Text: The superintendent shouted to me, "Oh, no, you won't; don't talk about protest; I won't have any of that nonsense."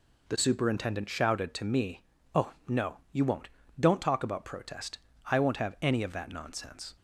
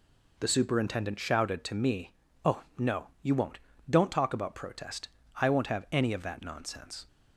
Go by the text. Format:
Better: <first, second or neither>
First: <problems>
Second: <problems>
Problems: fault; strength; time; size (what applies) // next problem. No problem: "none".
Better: neither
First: none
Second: none